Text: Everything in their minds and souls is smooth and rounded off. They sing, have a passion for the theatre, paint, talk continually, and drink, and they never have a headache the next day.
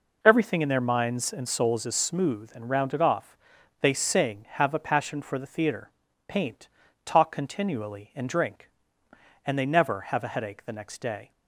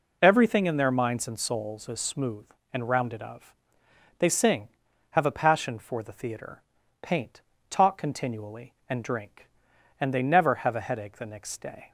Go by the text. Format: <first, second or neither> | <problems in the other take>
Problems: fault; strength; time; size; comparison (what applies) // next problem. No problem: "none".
first | says "of" for "off"; at 3.2 s